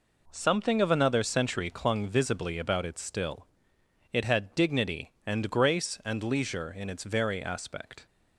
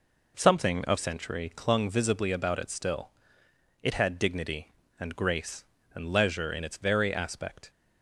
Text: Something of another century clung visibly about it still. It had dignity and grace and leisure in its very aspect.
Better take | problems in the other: first | skips "another"; at 0.9 s

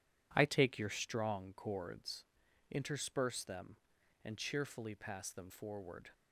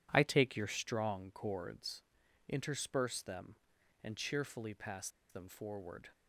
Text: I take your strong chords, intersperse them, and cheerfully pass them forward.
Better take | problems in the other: first | pauses between "pass" and "them"; slight; at 5.0 s; 0.21 s long

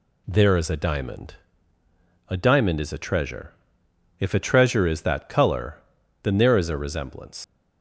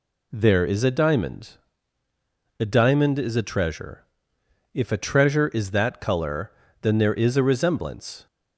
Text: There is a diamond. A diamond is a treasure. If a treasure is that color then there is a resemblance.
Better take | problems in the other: second | pauses between "color" and "then"; at 5.7 s; 0.44 s long; slight in the second // leaves "resemblance" unfinished; at 7.4 s; 100 ms

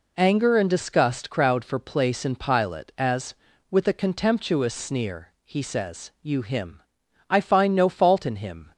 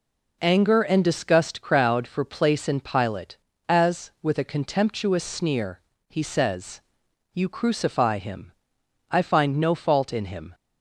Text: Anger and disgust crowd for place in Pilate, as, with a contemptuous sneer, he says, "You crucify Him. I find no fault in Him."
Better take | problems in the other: second | skips "crucify"; at 6.4 s

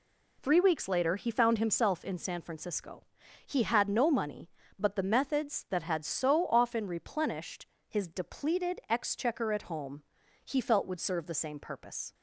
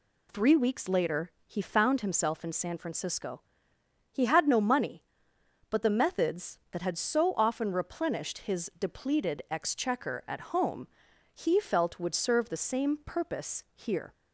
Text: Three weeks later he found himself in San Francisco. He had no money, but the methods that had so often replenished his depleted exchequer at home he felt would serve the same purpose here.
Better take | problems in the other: second | pauses between "replenished" and "his"; slight; at 7.6 s; 0.22 s long // pauses between "home" and "he"; at 10.0 s; 0.44 s long; also in the second // stops before "here"; at 12.1 s

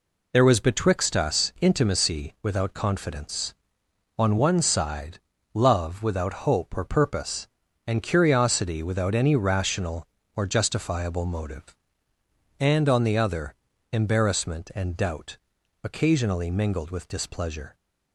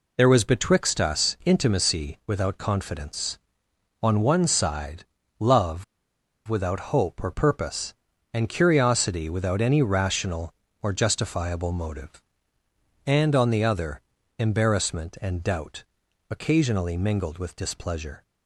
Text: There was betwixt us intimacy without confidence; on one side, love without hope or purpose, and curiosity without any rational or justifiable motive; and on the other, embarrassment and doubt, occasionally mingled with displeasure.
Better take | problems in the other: first | pauses between "love" and "without"; noticeable; at 5.8 s; 0.63 s long

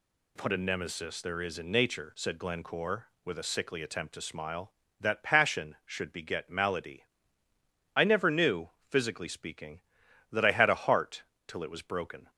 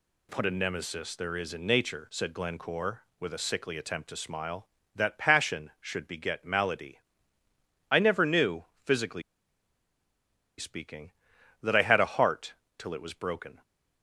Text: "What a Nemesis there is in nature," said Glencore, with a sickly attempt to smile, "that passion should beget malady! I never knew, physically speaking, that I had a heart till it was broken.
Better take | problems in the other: first | pauses between "physically" and "speaking"; strong; at 9.2 s; 1.3 s long // pauses between "heart" and "till"; slight; at 12.5 s; 0.24 s long; slight in the first

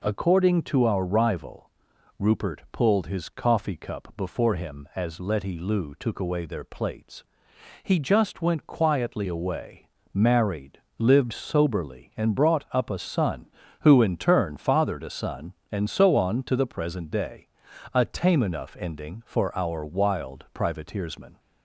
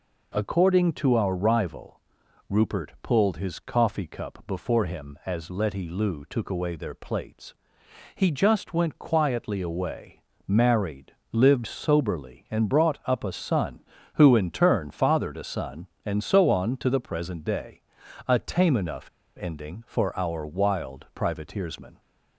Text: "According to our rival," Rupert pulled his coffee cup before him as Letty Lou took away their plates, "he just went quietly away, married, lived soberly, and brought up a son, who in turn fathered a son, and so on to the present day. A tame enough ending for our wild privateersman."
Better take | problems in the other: first | pauses between "enough" and "ending"; slight; at 19.0 s; 0.31 s long

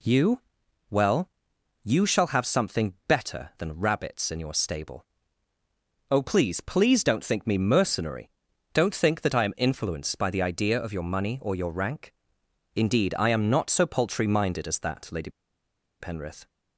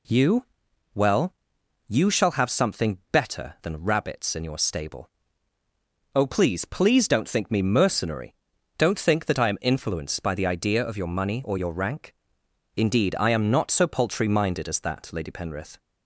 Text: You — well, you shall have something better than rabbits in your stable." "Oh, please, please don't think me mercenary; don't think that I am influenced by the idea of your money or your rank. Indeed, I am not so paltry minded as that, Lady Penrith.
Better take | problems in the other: second | pauses between "Lady" and "Penrith"; noticeable; at 15.2 s; 0.70 s long

